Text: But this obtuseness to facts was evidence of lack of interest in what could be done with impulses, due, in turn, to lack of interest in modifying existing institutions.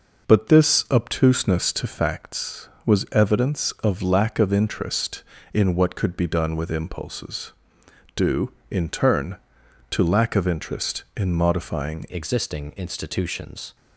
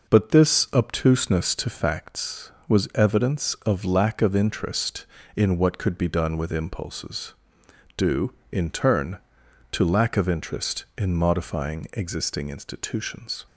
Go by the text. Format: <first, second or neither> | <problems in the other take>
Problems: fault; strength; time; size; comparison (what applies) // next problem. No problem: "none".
second | changes voice at "existing"; from 12.0 s on; 1.7 s long